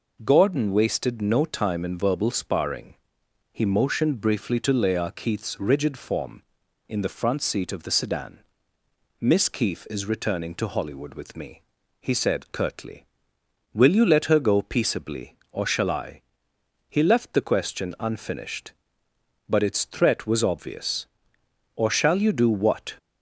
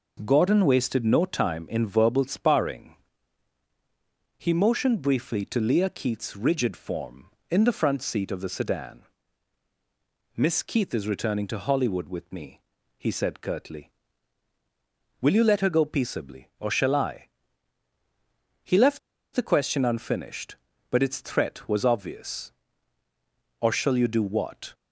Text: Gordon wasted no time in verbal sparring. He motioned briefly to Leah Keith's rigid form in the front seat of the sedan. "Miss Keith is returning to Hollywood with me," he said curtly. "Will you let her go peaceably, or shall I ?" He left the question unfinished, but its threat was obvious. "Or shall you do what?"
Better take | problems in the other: first | pauses between "left" and "the"; at 18.9 s; 0.36 s long

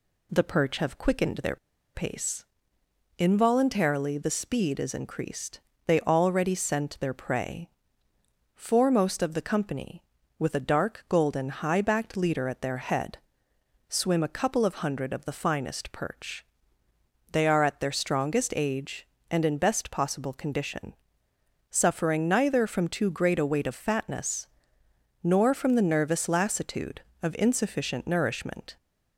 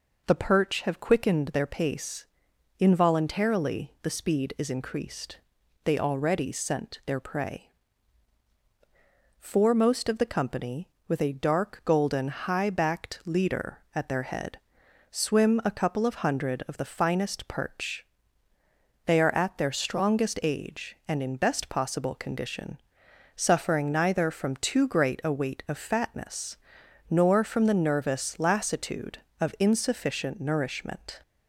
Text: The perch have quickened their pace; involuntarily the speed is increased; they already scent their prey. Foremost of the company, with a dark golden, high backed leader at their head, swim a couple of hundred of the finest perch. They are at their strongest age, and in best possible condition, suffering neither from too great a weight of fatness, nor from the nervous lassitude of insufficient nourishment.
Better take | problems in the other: second | pauses between "their" and "pace"; at 1.5 s; 0.38 s long

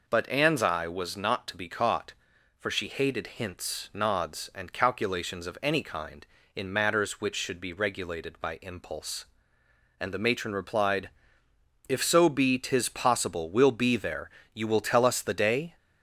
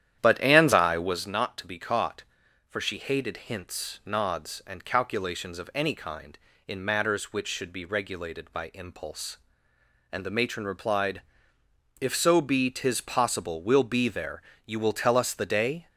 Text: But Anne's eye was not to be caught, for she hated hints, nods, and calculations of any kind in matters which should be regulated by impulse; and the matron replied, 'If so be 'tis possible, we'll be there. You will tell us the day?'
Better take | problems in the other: first | starts louder than the rest; strong; until 1.3 s; 10.5 dB

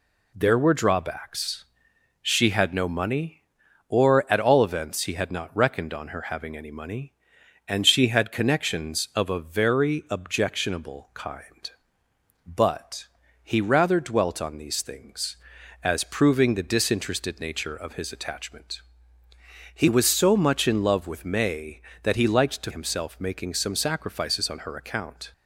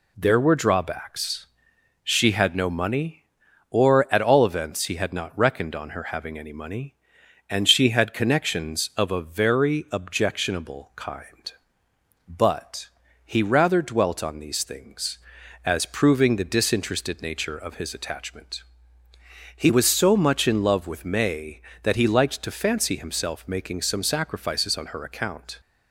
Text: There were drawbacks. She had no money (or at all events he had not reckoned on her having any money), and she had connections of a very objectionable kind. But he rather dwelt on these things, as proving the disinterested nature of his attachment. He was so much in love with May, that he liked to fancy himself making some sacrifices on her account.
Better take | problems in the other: second | pauses between "But" and "he"; at 13.0 s; 0.38 s long; also in the second // skips "fancy"; at 22.7 s

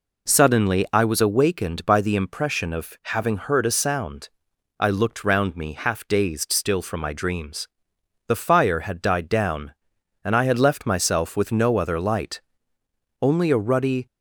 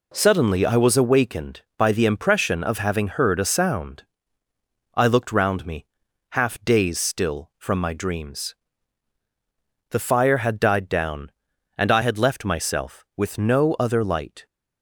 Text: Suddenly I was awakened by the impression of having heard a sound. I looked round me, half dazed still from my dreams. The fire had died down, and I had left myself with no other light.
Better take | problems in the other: second | goes on to say "Only a ruddy"; noticeable; from 13.1 s on; 0.86 s long

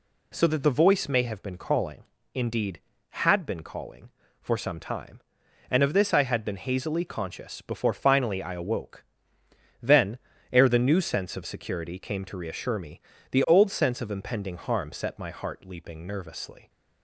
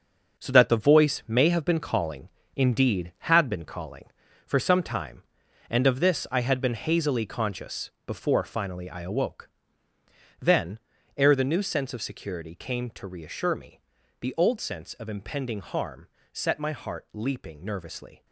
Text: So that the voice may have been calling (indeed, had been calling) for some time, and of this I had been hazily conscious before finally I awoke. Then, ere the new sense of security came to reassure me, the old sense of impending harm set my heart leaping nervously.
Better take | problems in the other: first | gets quieter; strong; throughout; 9 dB // pauses between "conscious" and "before"; slight; at 7.8 s; 0.16 s long // pauses between "harm" and "set"; slight; at 16.0 s; 0.26 s long

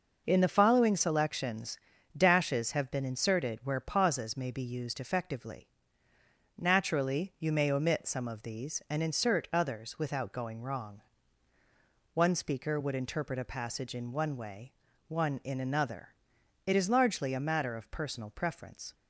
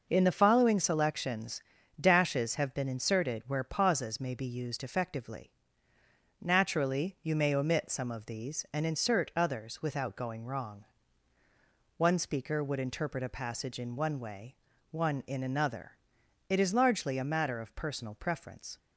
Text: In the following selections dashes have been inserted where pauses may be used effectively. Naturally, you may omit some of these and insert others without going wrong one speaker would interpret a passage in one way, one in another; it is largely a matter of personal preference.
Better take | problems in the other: neither | pauses between "selections" and "dashes"; slight; the same in both // pauses between "wrong" and "one"; the same in both

